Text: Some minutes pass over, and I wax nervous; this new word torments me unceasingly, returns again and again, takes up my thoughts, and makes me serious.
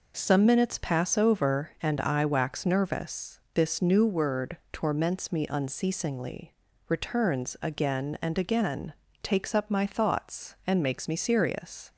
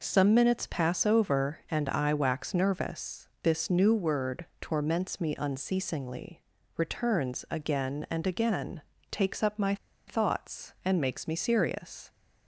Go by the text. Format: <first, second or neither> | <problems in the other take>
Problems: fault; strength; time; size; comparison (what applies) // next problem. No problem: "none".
first | pauses between "my" and "thoughts"; slight; at 9.7 s; 0.31 s long